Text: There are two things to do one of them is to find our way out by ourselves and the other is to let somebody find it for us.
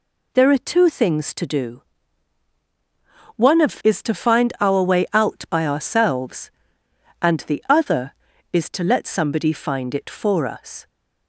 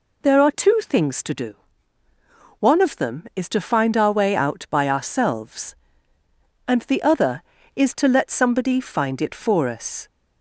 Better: second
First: pauses between "do" and "one"; strong; at 1.8 s; 1.5 s long // skips "them"; at 3.8 s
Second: pauses between "do" and "one"; at 1.5 s; 1.0 s long

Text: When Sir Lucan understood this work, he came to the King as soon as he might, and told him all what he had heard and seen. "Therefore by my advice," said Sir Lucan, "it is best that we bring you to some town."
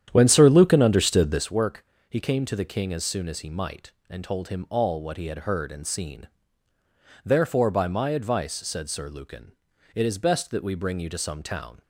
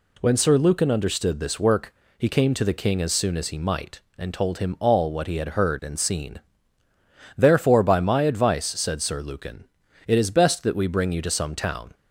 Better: second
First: starts louder than the rest; strong; until 1.5 s; 10 dB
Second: none

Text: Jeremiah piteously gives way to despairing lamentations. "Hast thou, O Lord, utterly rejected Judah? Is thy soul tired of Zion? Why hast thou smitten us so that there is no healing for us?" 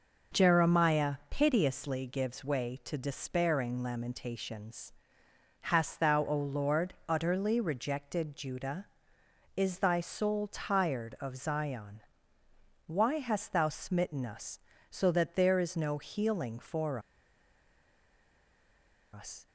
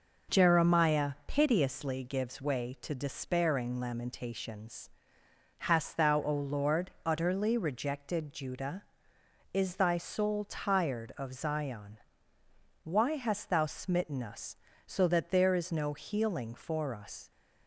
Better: second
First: pauses between "for" and "us"; strong; at 16.9 s; 2.1 s long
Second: none

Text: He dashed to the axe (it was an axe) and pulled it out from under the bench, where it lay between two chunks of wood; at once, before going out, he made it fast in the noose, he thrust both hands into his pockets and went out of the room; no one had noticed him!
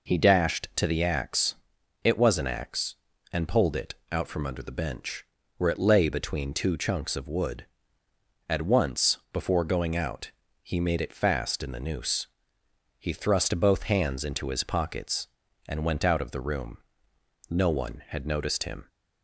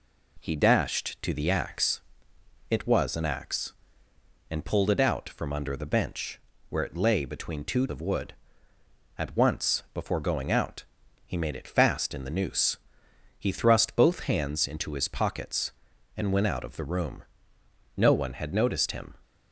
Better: first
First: none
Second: skips "chunks"; at 7.8 s

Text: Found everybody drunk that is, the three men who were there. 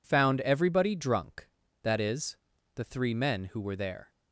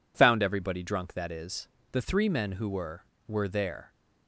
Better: first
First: none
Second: says "were" twice; at 3.2 s

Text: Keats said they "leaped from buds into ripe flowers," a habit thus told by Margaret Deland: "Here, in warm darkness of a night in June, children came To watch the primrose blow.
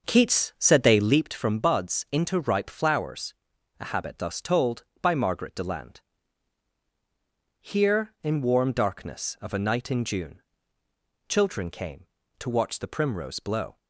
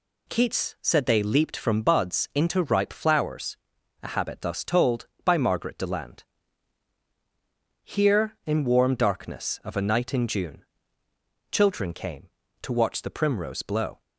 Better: second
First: starts louder than the rest; until 1.3 s; 6 dB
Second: none

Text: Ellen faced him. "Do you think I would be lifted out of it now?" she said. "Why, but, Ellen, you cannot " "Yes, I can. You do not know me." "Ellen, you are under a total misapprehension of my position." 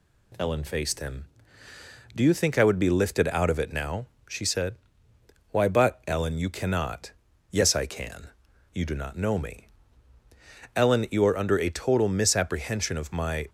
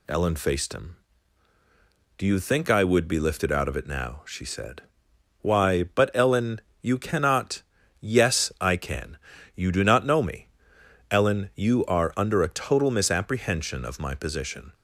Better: second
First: stops before "position"; at 13.4 s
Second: none

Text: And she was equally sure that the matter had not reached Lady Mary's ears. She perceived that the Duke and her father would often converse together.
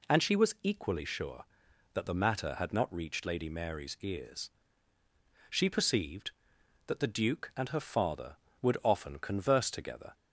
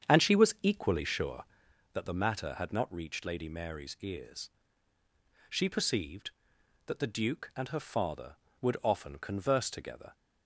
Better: first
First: none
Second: starts louder than the rest; strong; until 1.8 s; 8 dB

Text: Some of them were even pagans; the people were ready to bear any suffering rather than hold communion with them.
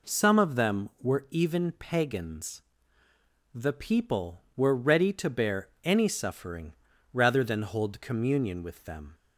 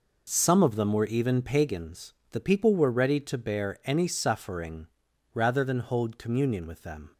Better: neither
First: pauses between "suffering" and "rather"; at 6.7 s; 0.40 s long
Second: pauses between "suffering" and "rather"; noticeable; at 4.8 s; 0.46 s long

